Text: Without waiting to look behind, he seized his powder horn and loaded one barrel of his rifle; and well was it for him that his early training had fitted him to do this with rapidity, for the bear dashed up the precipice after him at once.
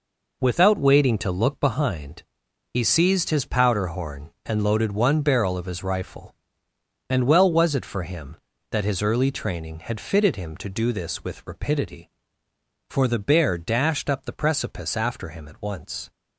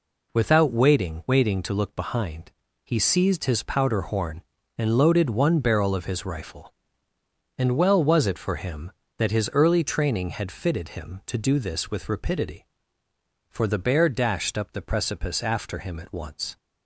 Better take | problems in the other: first | says "waiting" twice; at 1.2 s

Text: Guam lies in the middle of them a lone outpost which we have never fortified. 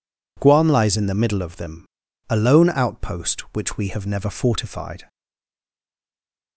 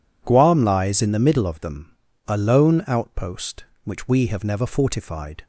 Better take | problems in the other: second | pauses between "them" and "a"; at 1.8 s; 0.44 s long; slight in the second // stays silent after the last word; noticeable; from 5.0 s on; 1.5 s long

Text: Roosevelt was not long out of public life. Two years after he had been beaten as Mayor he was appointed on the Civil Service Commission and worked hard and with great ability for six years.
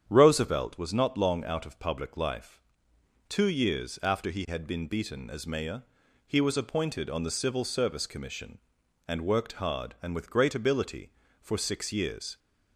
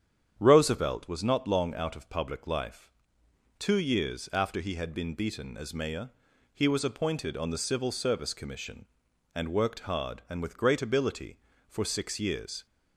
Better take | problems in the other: neither | starts louder than the rest; strong; the same in both // pauses between "Mayor" and "he"; the same in both

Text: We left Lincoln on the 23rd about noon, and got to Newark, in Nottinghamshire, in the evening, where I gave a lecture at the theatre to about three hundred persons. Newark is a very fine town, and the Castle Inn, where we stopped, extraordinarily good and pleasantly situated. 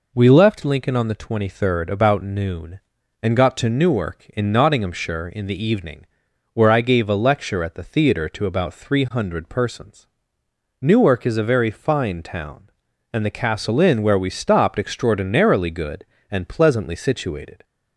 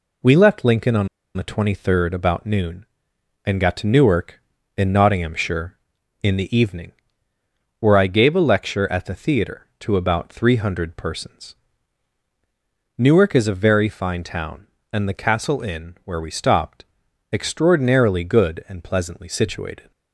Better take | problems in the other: first | pauses between "on" and "the"; slight; at 1.0 s; 0.29 s long

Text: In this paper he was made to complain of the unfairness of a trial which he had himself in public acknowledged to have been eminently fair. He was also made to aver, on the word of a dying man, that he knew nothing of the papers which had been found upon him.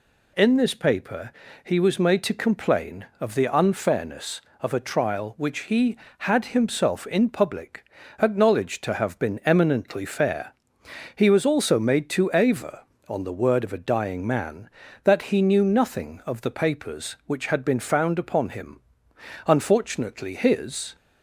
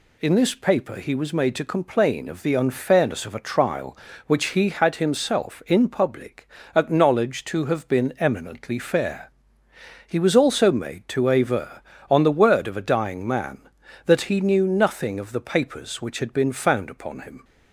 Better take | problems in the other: second | pauses between "paper" and "he"; slight; at 1.3 s; 0.32 s long // pauses between "public" and "acknowledged"; slight; at 7.8 s; 0.36 s long; slight in the second // goes on to say "Unfortunately his"; from 19.4 s on; 1.5 s long

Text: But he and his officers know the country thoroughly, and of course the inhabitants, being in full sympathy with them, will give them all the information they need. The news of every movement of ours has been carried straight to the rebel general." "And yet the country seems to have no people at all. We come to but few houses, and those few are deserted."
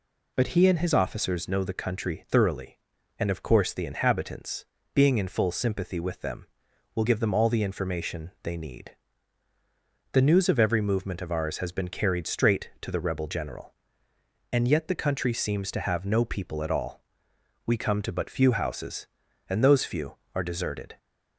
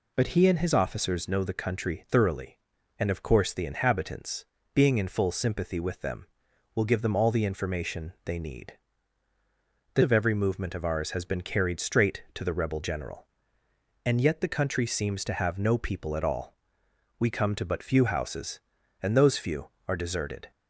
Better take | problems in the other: first | skips "news"; at 10.0 s

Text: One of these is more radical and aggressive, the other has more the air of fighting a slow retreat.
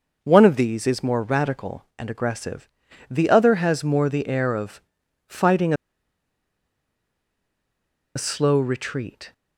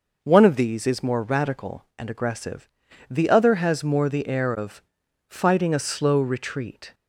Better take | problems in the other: second | pauses between "of" and "fighting"; noticeable; at 4.8 s; 0.46 s long; noticeable in the second // pauses between "fighting" and "a"; strong; at 5.7 s; 2.4 s long

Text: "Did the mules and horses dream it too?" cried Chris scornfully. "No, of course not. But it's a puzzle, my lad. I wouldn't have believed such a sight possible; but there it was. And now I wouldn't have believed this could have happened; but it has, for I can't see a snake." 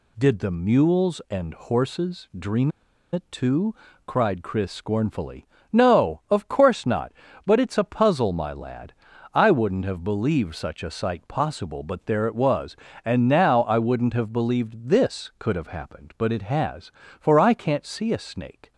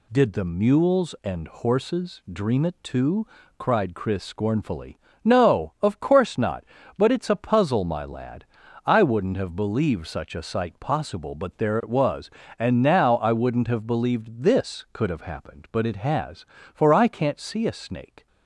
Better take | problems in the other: second | pauses between "dream" and "it"; at 2.7 s; 0.42 s long

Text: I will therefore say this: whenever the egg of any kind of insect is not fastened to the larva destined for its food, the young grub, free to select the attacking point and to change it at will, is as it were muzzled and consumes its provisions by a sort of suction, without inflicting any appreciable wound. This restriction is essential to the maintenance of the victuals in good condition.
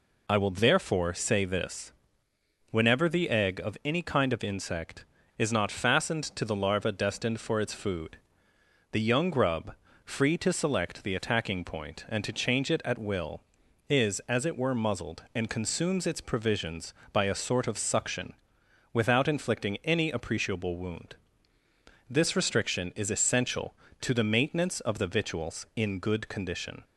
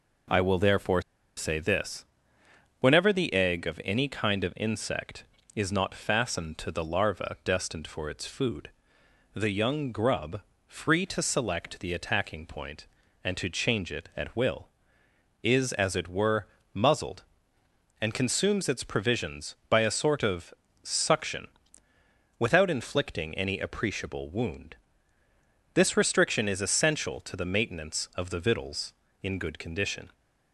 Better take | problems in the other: first | pauses between "therefore" and "say"; at 1.0 s; 0.36 s long // pauses between "were" and "muzzled"; slight; at 16.4 s; 0.26 s long // pauses between "of" and "suction"; slight; at 20.5 s; 0.28 s long

